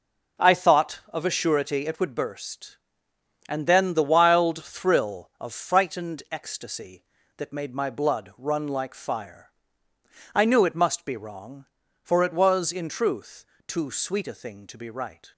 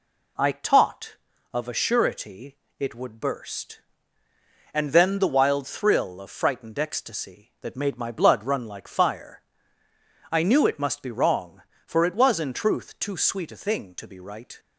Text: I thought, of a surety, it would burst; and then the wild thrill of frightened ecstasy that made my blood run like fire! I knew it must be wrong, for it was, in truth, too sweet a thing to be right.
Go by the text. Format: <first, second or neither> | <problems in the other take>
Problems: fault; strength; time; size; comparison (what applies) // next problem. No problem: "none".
first | says "taught" for "thought"; at 0.5 s